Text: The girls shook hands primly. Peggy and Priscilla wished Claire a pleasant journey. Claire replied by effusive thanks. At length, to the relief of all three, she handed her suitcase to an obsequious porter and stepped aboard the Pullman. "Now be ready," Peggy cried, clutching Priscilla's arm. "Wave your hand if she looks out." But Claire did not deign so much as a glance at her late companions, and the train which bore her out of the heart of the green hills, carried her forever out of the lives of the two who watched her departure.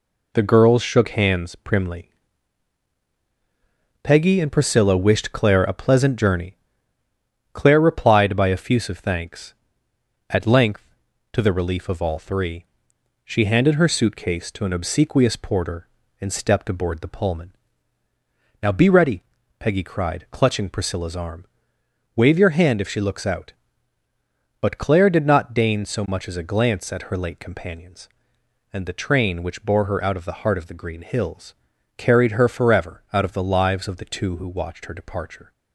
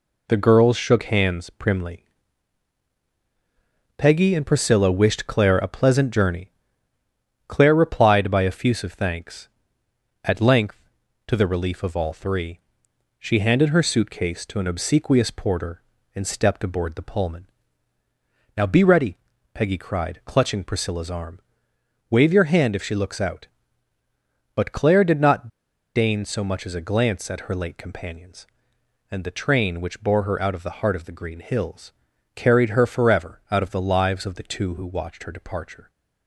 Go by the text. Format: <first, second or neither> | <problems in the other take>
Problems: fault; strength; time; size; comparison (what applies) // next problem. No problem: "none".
first | pauses between "not" and "deign"; noticeable; at 25.4 s; 0.47 s long